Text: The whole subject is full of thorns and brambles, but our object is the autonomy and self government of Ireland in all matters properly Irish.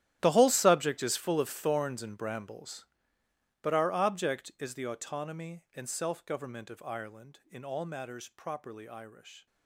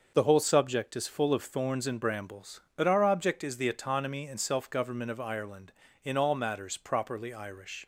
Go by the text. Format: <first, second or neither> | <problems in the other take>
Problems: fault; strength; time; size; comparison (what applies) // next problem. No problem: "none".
second | gets quieter; strong; throughout; 18 dB // starts louder than the rest; strong; until 1.2 s; 12 dB; also in the second